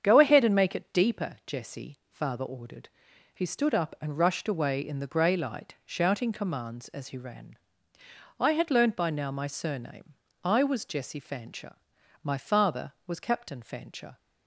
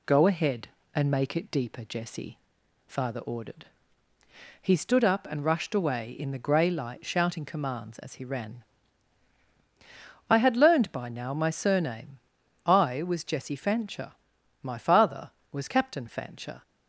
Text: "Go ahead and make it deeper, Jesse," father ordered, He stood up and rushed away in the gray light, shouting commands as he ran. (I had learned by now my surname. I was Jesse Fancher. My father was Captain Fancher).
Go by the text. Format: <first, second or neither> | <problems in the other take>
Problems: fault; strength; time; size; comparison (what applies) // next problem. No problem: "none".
second | starts louder than the rest; strong; until 1.4 s; 7.5 dB